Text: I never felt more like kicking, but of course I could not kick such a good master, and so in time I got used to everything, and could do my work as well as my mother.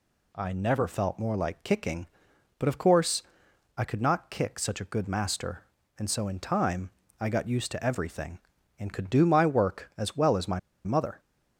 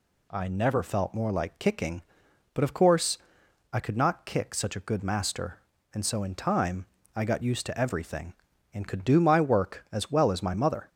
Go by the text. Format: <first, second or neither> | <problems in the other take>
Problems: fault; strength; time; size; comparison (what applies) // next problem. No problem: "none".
second | pauses between "course" and "I"; noticeable; at 3.2 s; 0.54 s long; noticeable in the second // pauses between "time" and "I"; slight; at 6.9 s; 0.28 s long; slight in the second // pauses between "my" and "mother"; slight; at 10.5 s; 0.26 s long